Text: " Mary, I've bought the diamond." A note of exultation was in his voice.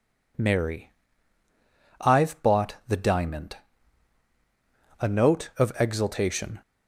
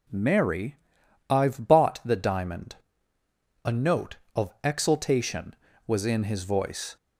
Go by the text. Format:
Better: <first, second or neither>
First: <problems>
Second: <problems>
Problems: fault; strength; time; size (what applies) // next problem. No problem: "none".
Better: second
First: stops before "was in his voice"; at 6.6 s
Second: none